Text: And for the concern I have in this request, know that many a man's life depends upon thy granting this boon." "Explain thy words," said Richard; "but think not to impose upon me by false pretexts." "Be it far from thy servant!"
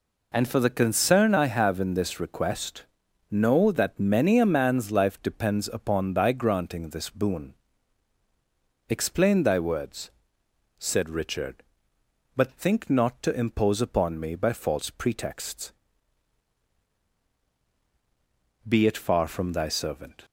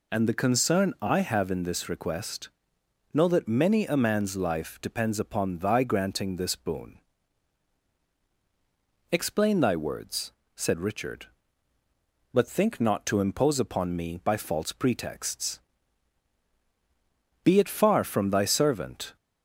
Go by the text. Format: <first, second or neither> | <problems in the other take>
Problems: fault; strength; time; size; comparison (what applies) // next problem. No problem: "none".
first | skips "for"; at 0.2 s